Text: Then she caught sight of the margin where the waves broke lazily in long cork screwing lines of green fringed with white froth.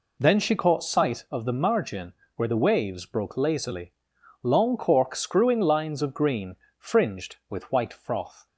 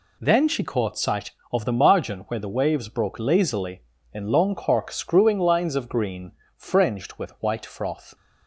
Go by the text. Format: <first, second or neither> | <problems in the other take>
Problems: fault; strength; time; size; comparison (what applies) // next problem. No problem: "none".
second | pauses between "margin" and "where"; slight; at 2.1 s; 0.24 s long // skips "in"; at 4.1 s // pauses between "green" and "fringed"; slight; at 6.5 s; 0.24 s long; slight in the second